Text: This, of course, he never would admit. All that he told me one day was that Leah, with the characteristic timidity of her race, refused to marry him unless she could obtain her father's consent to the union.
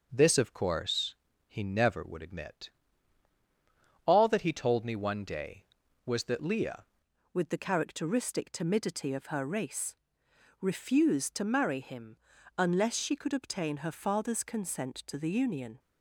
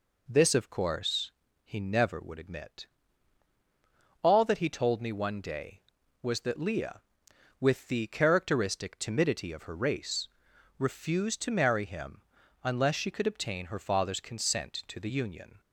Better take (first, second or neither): second